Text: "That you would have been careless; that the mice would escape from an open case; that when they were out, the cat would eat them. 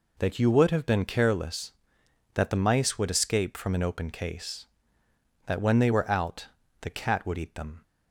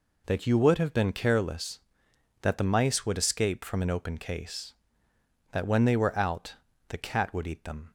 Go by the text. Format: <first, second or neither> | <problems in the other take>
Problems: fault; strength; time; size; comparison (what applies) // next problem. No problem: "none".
neither | none